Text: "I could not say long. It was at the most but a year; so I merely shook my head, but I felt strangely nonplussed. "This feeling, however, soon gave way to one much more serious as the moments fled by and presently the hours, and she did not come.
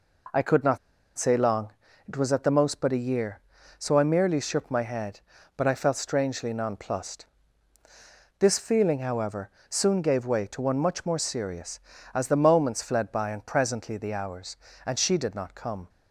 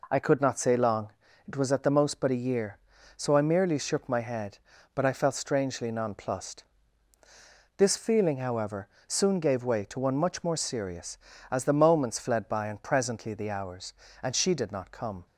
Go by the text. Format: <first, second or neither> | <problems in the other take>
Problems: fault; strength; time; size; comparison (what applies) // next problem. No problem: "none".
second | pauses between "not" and "say"; at 0.7 s; 0.40 s long